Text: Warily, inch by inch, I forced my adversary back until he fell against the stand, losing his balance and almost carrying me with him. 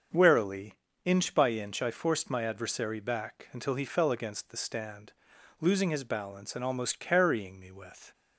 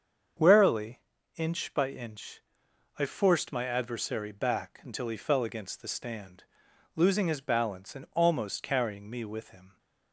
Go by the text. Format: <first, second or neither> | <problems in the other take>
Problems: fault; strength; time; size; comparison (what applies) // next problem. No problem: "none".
second | starts louder than the rest; until 1.4 s; 7 dB; also in the second // stops before "him"; at 8.1 s